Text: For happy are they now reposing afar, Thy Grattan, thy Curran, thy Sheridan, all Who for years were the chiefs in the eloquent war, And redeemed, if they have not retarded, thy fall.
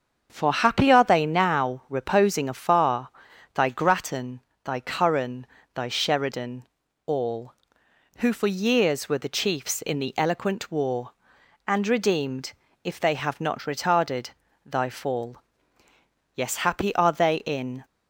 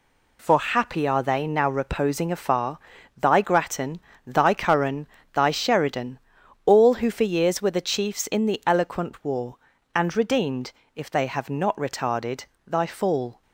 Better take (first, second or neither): second